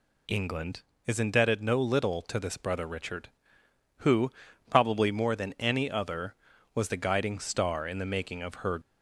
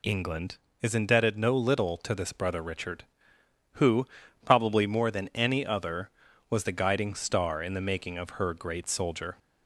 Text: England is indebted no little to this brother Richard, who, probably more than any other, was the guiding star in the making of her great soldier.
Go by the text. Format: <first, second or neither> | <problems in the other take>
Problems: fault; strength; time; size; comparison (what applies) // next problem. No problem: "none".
second | stops before "great soldier"; at 8.8 s